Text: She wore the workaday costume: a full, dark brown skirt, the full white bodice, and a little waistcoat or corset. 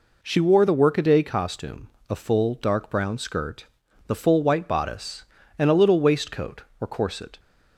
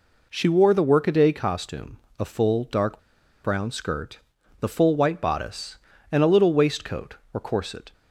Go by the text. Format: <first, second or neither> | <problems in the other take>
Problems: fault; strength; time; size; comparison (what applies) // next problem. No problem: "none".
first | pauses between "dark" and "brown"; at 2.9 s; 0.45 s long